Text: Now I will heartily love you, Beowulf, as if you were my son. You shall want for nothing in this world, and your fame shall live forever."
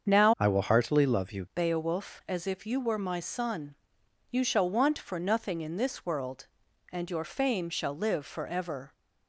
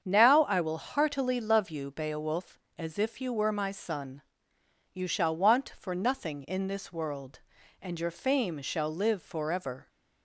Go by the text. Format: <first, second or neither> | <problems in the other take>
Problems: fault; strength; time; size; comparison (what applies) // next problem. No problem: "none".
second | starts louder than the rest; strong; until 1.1 s; 7 dB; strong in the second // changes voice from "I" to "you"; from 0.3 to 1.4 s; 1.1 s long